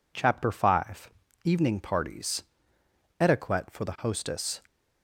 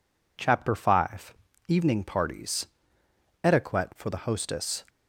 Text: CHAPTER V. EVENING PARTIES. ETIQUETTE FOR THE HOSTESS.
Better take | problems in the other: neither | none

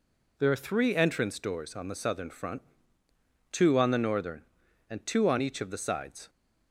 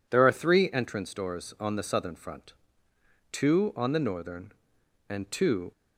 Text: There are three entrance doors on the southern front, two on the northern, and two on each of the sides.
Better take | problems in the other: first | stops before "on each of the sides"; at 5.7 s

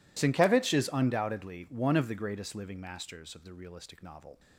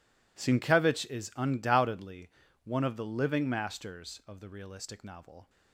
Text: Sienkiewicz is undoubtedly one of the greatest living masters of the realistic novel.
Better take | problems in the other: first | pauses between "undoubtedly" and "one"; slight; at 2.2 s; 0.34 s long // skips "greatest"; at 3.0 s

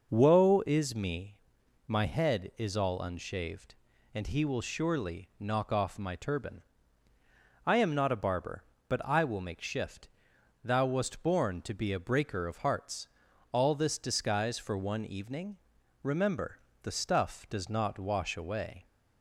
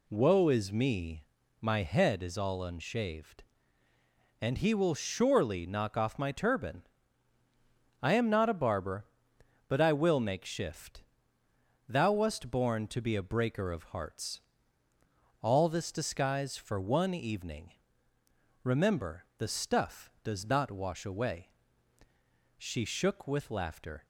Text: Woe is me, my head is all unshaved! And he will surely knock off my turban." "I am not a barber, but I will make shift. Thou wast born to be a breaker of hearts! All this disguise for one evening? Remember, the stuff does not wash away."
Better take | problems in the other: first | goes on to say "She shook with laughter"; from 22.5 s on; 1.4 s long

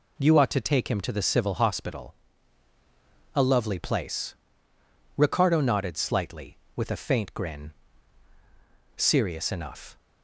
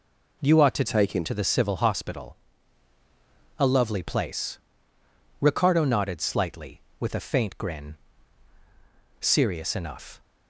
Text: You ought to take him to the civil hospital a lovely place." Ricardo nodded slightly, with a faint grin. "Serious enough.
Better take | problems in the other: first | changes voice from "take" to "him"; from 0.8 to 1.2 s; 0.4 s long // pauses between "hospital" and "a"; at 2.3 s; 1.2 s long; also in the first

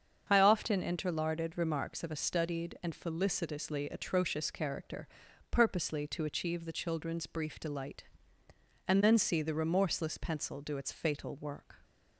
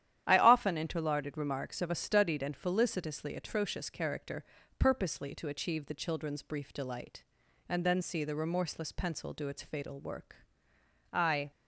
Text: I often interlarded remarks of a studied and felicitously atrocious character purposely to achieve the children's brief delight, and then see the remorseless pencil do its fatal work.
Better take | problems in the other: first | starts louder than the rest; strong; until 1.2 s; 11 dB; strong in the first // pauses between "character" and "purposely"; slight; at 4.4 s; 0.34 s long; also in the first // goes on to say "I"; slight; from 11.1 s on; 0.38 s long

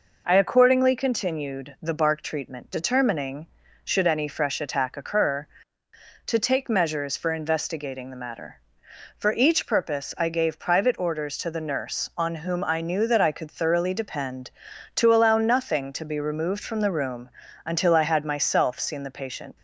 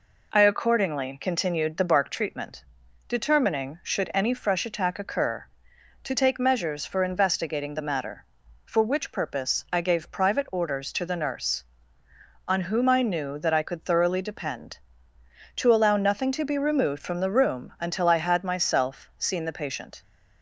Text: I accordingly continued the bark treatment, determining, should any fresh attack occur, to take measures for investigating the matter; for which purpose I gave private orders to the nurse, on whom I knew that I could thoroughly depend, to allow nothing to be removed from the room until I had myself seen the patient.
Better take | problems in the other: second | says "each" for "which"; at 9.3 s // pauses between "room" and "until"; slight; at 17.2 s; 0.34 s long

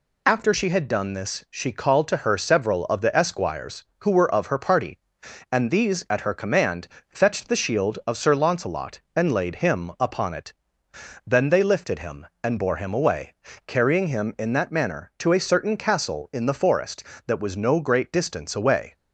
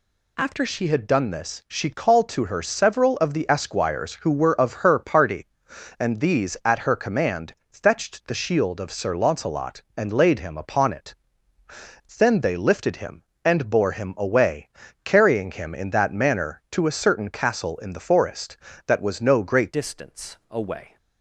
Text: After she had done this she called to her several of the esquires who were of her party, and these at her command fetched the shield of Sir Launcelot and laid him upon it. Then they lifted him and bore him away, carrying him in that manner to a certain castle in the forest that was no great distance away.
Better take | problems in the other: first | pauses between "command" and "fetched"; slight; at 7.5 s; 0.16 s long; slight in the first // changes voice at "distance"; from 19.7 s on; 1.2 s long

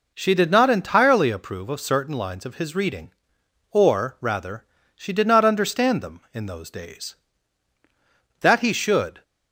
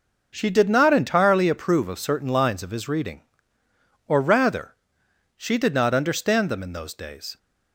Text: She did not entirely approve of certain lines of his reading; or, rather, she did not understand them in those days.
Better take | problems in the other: second | goes on to say "That he should"; noticeable; from 8.3 s on; 0.84 s long

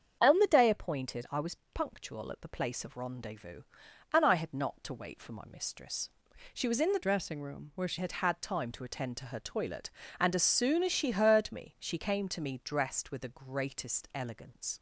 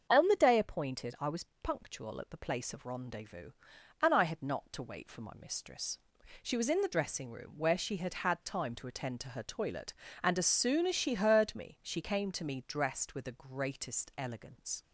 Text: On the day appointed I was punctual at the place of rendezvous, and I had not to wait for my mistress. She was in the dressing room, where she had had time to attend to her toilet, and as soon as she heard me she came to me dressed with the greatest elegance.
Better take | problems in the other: second | starts louder than the rest; strong; until 1.2 s; 7.5 dB; also in the second // pauses between "was" and "punctual"; slight; at 1.5 s; 0.18 s long; slight in the second // changes voice from "dressing" to "she"; from 7.0 to 7.9 s; 0.9 s long

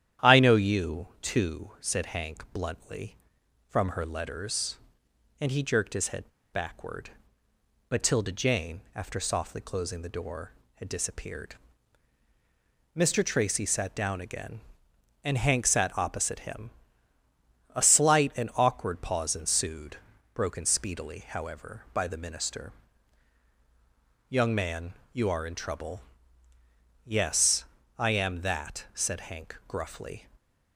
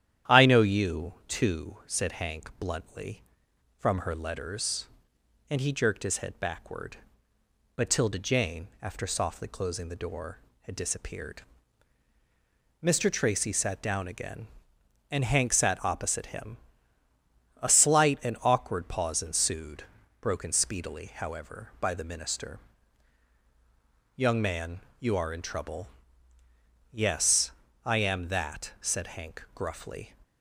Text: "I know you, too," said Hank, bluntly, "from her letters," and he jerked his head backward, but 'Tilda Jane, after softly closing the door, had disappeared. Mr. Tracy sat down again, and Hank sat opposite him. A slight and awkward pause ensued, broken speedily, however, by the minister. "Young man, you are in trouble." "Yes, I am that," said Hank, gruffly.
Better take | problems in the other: second | starts louder than the rest; strong; until 1.3 s; 10.5 dB; strong in the second // pauses between "head" and "backward"; slight; at 6.2 s; 0.23 s long

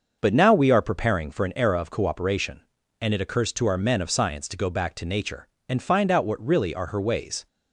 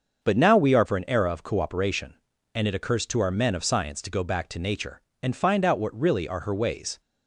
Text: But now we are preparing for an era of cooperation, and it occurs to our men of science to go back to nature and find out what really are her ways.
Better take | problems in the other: first | starts louder than the rest; until 1.3 s; 6.5 dB; noticeable in the first // skips "preparing"; at 0.8 s

